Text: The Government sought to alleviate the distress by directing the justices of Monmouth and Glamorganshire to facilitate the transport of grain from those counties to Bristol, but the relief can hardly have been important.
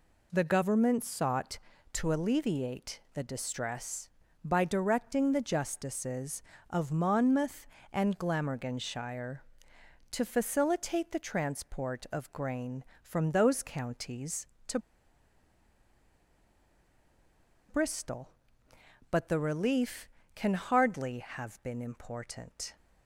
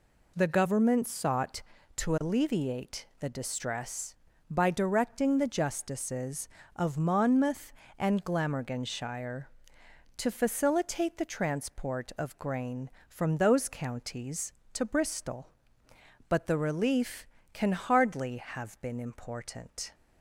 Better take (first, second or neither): second